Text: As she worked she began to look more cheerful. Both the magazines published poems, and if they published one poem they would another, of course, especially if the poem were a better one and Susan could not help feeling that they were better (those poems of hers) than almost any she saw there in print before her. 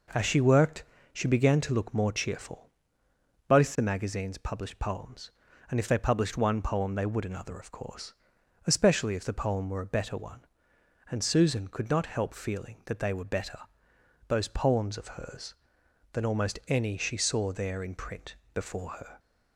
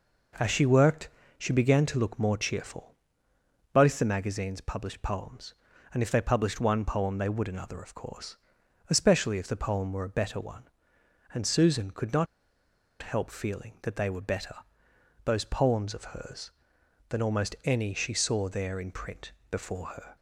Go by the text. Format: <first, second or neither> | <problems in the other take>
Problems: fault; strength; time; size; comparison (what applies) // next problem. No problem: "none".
first | pauses between "worked" and "she"; slight; at 1.0 s; 0.30 s long; slight in the first // pauses between "not" and "help"; noticeable; at 12.2 s; 0.75 s long // pauses between "print" and "before"; slight; at 19.3 s; 0.18 s long; slight in the first